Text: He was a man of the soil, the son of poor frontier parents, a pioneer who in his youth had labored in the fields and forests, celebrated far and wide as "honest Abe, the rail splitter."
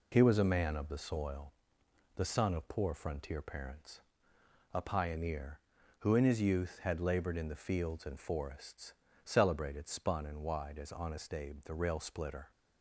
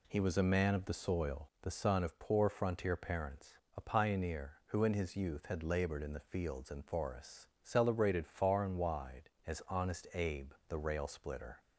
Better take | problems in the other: second | says "spun" for "far"; at 9.8 s

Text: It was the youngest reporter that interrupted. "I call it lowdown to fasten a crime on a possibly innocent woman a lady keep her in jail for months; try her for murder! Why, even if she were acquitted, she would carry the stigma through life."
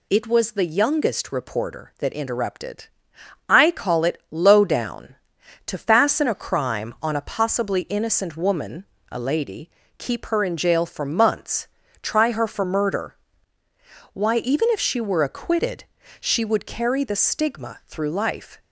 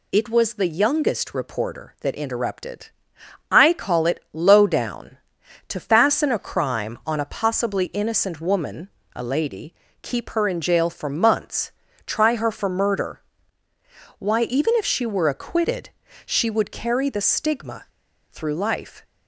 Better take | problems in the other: first | pauses between "woman" and "a"; slight; at 8.8 s; 0.30 s long; slight in the first // pauses between "lady" and "keep"; slight; at 9.7 s; 0.30 s long; slight in the first // pauses between "stigma" and "through"; noticeable; at 17.8 s; 0.46 s long

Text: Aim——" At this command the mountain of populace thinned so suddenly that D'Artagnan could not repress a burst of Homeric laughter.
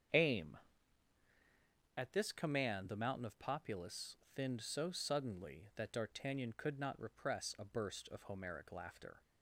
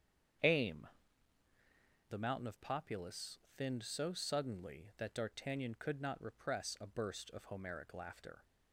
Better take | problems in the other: first | starts louder than the rest; strong; until 2.7 s; 8 dB; strong in the first // skips "At this command"; at 1.4 s // pauses between "populace" and "thinned"; slight; at 3.3 s; 0.20 s long; slight in the first

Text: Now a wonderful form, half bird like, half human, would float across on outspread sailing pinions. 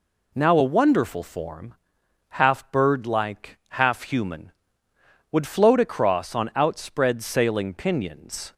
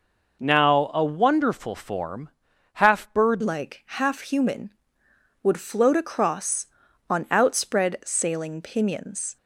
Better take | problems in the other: first | changes voice at "like"; from 3.4 s on; 5.9 s long

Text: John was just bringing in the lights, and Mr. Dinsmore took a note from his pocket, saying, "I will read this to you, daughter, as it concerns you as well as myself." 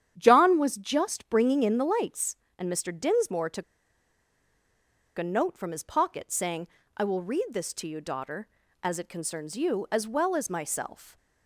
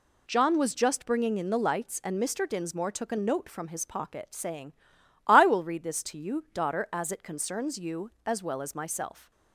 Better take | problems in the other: second | starts louder than the rest; strong; until 1.1 s; 9.5 dB // pauses between "took" and "a"; strong; at 3.6 s; 1.5 s long

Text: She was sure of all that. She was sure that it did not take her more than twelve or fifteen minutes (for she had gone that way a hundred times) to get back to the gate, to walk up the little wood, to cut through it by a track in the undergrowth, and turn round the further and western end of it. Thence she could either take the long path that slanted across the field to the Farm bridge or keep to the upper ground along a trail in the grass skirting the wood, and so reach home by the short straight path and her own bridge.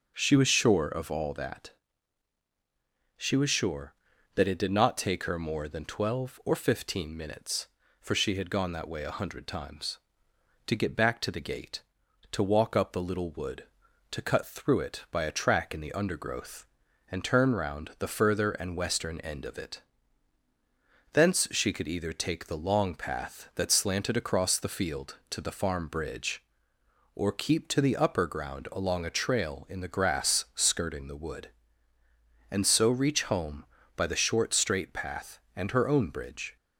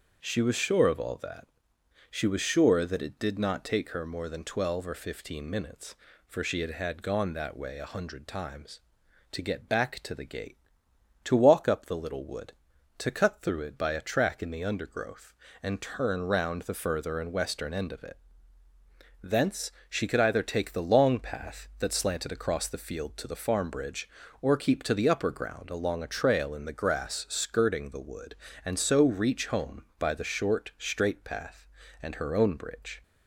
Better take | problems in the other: first | starts louder than the rest; strong; until 1.2 s; 7 dB // says "had" twice; at 6.7 s // pauses between "Thence" and "she"; slight; at 19.7 s; 0.18 s long

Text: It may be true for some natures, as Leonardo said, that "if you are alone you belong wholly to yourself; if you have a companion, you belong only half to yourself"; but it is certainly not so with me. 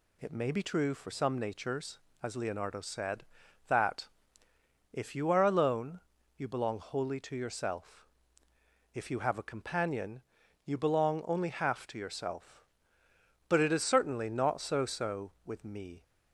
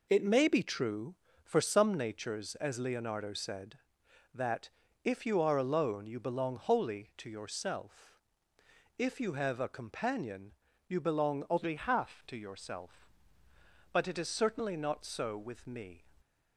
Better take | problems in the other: second | pauses between "that" and "if"; noticeable; at 4.0 s; 0.82 s long; slight in the second // pauses between "alone" and "you"; slight; at 6.0 s; 0.36 s long // says "so" twice; at 14.8 s

